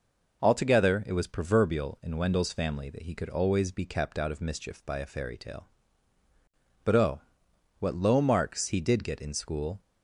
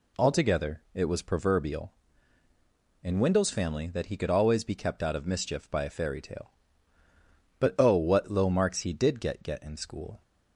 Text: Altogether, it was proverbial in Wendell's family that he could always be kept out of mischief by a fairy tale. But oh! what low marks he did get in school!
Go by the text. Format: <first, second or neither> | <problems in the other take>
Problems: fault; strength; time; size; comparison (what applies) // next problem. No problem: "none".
first | says "get" twice; at 9.4 s